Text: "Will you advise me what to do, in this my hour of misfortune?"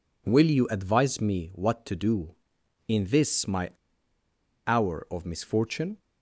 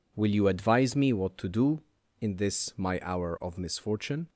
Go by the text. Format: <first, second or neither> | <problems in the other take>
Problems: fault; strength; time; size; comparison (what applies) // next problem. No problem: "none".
second | pauses between "my" and "hour"; noticeable; at 3.6 s; 0.96 s long